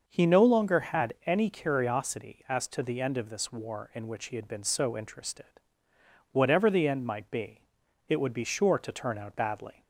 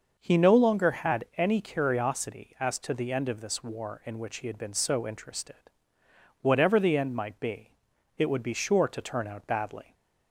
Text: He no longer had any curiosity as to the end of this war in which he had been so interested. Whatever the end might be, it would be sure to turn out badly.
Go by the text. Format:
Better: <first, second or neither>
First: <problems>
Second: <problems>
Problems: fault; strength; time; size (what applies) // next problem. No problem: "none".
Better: neither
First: starts louder than the rest; noticeable; until 1.0 s; 6 dB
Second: starts louder than the rest; noticeable; until 1.2 s; 6 dB